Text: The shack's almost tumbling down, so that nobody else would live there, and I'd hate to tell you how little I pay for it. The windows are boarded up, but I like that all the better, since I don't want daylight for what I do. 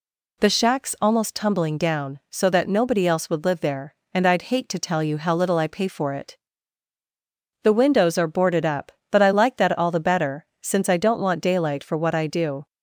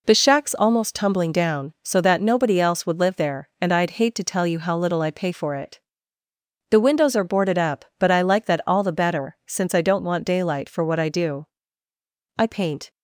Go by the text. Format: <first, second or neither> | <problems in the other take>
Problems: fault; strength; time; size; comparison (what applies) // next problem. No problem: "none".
first | goes on to say "I paint"; from 12.3 s on; 0.52 s long